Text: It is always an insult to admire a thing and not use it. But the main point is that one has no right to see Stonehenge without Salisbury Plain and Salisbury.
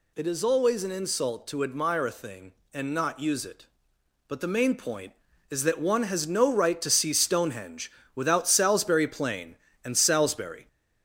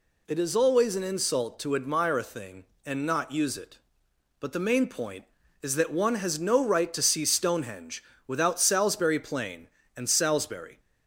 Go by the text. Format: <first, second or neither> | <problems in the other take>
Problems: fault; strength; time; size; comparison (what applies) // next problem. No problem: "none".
second | gets louder; slight; throughout; 2.5 dB // pauses between "Stonehenge" and "without"; slight; at 7.9 s; 0.22 s long; slight in the second